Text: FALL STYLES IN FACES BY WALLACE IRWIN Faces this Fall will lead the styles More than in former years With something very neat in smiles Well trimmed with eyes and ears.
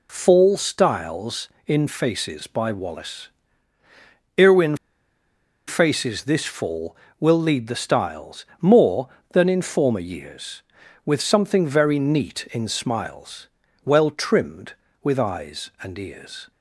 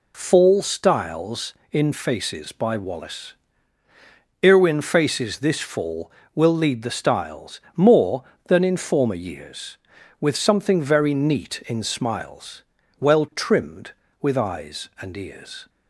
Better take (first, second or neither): second